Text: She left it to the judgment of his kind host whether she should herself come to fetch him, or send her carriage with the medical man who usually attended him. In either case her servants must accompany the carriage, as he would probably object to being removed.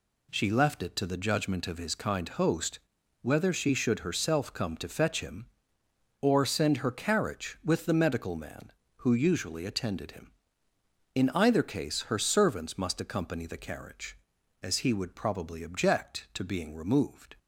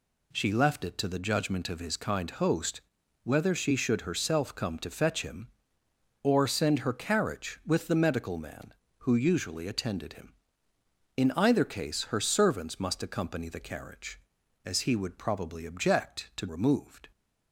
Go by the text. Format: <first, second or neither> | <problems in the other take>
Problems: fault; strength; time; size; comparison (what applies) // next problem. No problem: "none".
first | pauses between "host" and "whether"; at 2.7 s; 0.44 s long; also in the first // skips "being"; at 16.4 s